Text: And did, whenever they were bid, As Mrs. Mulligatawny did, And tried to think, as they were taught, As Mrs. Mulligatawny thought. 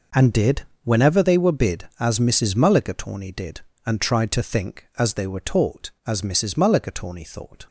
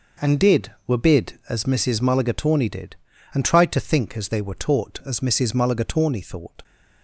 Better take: first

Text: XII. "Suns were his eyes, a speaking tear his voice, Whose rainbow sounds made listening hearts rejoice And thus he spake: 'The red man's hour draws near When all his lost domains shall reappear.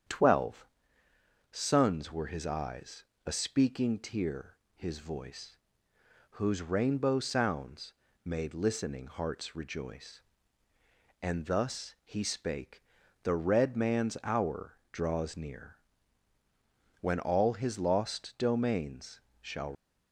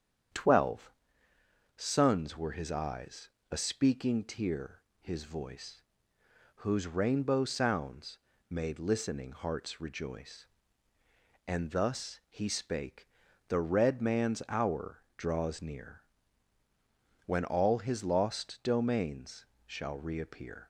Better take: second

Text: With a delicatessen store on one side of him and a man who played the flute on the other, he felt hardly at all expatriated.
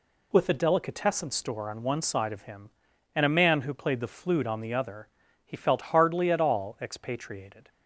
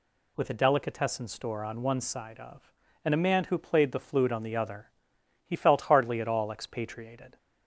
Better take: first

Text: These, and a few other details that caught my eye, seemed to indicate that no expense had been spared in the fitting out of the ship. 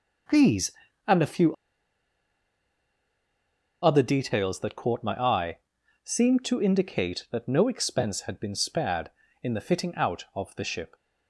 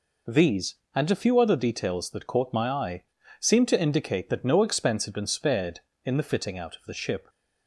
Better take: second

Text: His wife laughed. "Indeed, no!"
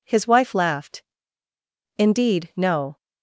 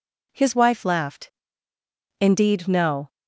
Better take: neither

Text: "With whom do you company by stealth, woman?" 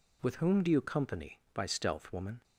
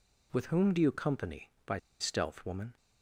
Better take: first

